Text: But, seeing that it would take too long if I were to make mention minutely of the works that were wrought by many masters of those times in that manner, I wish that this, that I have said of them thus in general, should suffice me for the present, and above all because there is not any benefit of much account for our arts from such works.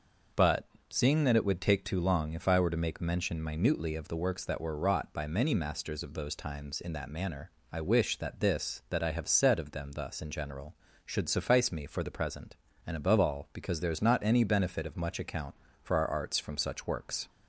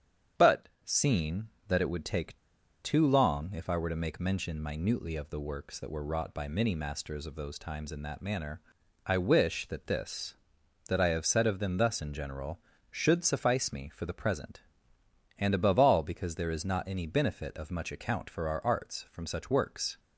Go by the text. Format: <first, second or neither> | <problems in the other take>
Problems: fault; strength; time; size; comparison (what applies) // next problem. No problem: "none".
first | starts louder than the rest; strong; until 1.7 s; 8 dB // pauses between "take" and "too"; at 2.3 s; 0.45 s long